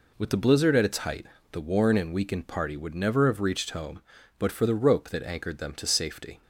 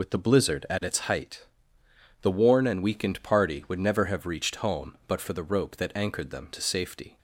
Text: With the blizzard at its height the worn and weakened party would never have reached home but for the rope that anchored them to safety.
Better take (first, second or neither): first